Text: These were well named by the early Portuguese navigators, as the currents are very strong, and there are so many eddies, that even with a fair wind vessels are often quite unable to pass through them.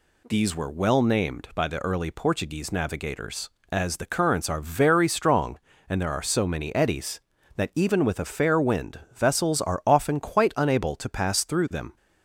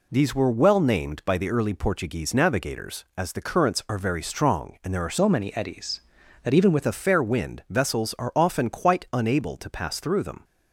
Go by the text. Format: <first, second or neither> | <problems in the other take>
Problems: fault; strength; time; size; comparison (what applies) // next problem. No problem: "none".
first | changes voice from "so" to "with"; from 5.1 to 6.8 s; 1.7 s long